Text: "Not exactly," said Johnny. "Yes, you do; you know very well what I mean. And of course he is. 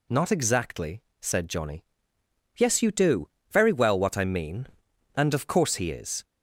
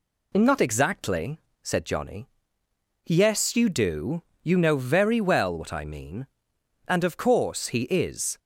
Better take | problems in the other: second | skips "you know"; at 3.3 s

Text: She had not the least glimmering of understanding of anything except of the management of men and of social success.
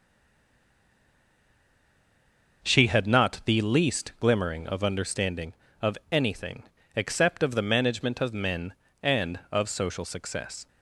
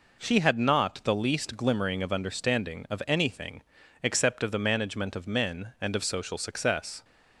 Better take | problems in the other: second | stays silent before the first word; strong; until 2.6 s; 2.6 s long // pauses between "anything" and "except"; slight; at 6.6 s; 0.32 s long; also in the second

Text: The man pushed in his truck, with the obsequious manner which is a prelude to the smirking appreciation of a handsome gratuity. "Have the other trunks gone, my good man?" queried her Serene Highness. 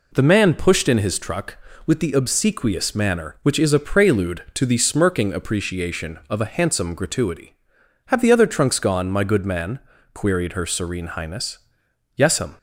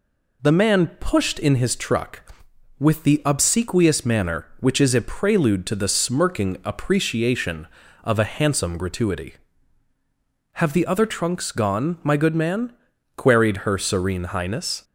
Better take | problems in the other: second | goes on to say "Yes'm"; slight; from 12.1 s on; 0.42 s long

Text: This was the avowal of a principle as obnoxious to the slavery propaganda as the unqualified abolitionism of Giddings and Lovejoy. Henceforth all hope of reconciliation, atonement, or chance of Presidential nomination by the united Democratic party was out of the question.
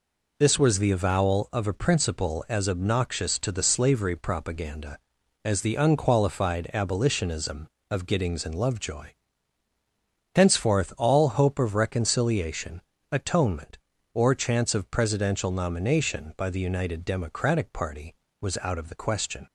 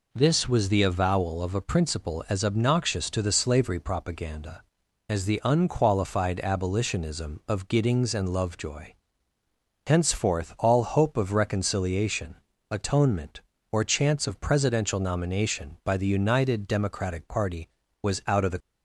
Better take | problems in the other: first | stops before "question"; at 18.6 s

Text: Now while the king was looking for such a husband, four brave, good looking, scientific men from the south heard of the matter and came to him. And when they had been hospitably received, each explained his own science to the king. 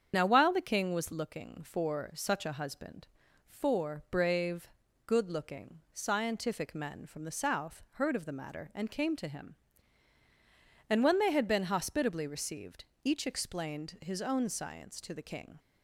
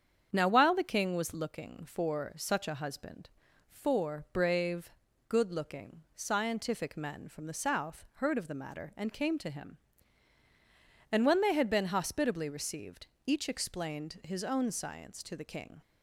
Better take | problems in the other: second | loses the start of "Now"; at 0.1 s; 30 ms // starts louder than the rest; strong; until 1.1 s; 7.5 dB; strong in the second

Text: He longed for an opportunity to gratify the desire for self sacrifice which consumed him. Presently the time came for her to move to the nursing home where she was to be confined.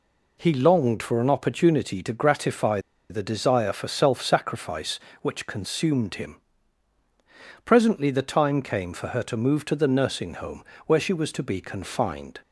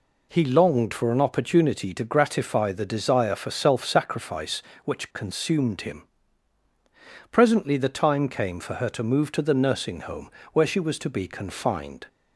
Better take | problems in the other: second | pauses between "gratify" and "the"; slight; at 2.7 s; 0.30 s long // pauses between "home" and "where"; slight; at 10.6 s; 0.20 s long; slight in the second

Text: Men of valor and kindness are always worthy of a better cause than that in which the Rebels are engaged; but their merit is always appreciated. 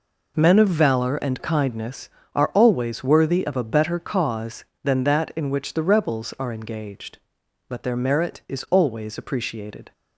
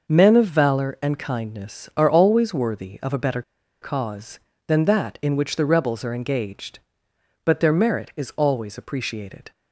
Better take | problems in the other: first | pauses between "better" and "cause"; at 3.4 s; 0.40 s long

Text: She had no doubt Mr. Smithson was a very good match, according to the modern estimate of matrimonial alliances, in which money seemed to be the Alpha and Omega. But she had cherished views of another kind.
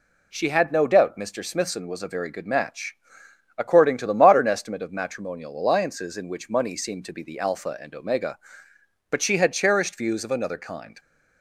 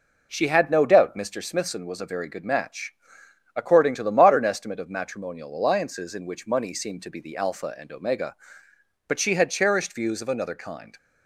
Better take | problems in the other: first | starts louder than the rest; noticeable; until 1.5 s; 4.5 dB

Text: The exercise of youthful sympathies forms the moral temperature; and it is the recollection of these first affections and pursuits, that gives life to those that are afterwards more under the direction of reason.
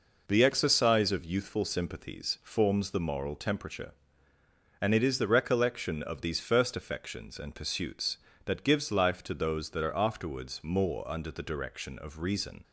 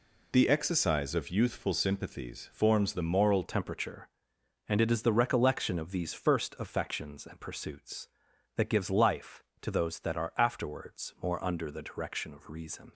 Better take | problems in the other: first | changes voice at "temperature"; from 3.4 s on; 9.5 s long

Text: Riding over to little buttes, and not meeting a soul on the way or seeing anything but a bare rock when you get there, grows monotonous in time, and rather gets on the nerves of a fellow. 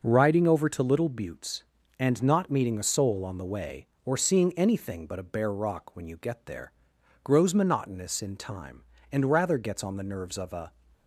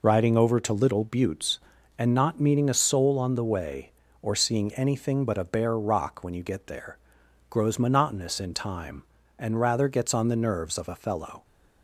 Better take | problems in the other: second | starts louder than the rest; until 1.0 s; 6 dB // stops before "fellow"; at 10.9 s

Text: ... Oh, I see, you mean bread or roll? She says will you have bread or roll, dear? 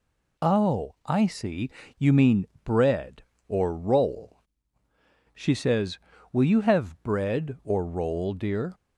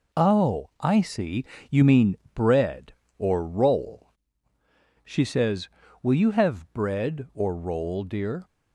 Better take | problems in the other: first | gets quieter; throughout; 6.5 dB // pauses between "mean" and "bread"; slight; at 2.1 s; 0.18 s long; slight in the first

